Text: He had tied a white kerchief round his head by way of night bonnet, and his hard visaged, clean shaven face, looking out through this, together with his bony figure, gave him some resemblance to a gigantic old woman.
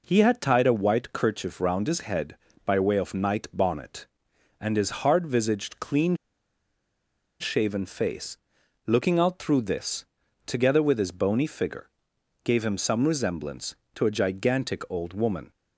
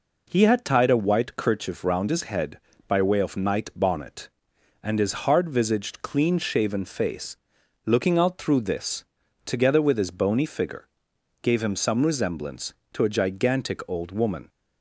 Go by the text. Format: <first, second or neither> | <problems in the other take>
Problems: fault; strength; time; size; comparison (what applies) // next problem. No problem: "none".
second | pauses between "clean" and "shaven"; strong; at 6.1 s; 1.2 s long